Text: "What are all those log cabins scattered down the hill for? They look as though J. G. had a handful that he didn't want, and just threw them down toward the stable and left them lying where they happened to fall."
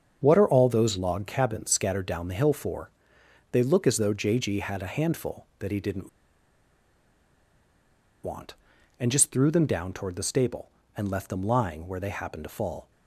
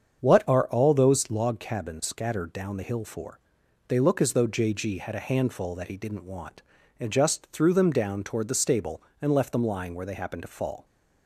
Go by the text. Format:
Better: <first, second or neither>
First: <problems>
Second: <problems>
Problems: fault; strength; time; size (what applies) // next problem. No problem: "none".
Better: second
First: starts louder than the rest; strong; until 1.2 s; 7 dB // pauses between "didn't" and "want"; strong; at 6.0 s; 2.1 s long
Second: starts louder than the rest; strong; until 1.2 s; 7.5 dB